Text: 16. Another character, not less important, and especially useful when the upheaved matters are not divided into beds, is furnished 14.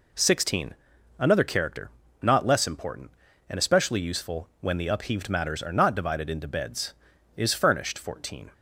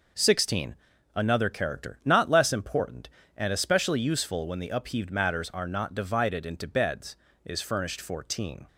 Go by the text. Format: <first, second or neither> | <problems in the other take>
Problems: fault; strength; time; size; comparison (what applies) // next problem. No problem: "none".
neither | none